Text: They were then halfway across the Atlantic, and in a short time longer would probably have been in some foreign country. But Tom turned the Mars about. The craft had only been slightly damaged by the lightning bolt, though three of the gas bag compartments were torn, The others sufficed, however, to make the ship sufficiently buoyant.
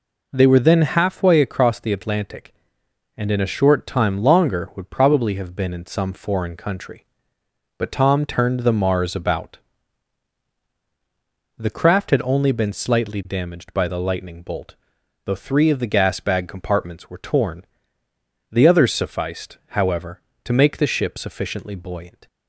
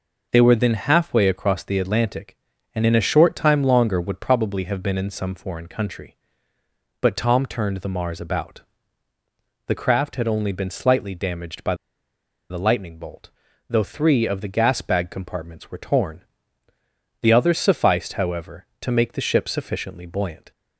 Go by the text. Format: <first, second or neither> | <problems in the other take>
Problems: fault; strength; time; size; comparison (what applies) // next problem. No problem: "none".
first | pauses between "by" and "the"; noticeable; at 11.7 s; 0.74 s long